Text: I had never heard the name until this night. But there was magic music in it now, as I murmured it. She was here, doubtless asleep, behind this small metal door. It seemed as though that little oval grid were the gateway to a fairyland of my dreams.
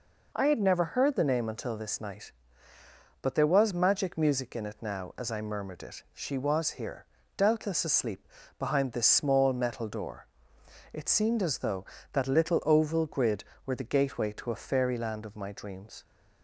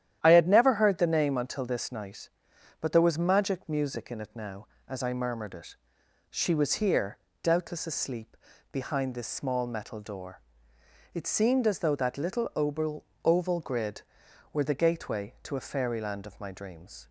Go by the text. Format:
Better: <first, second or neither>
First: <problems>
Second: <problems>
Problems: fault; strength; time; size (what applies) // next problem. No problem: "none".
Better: first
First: none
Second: starts louder than the rest; strong; until 1.2 s; 11 dB // says "oval" twice; at 13.2 s